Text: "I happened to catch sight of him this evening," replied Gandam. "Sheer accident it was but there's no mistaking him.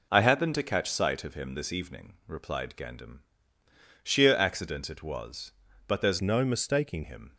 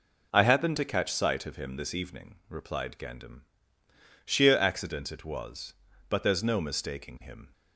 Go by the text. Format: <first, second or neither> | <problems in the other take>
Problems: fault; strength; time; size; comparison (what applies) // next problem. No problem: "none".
second | changes voice from "no" to "mistaking"; from 6.2 to 7.0 s; 0.8 s long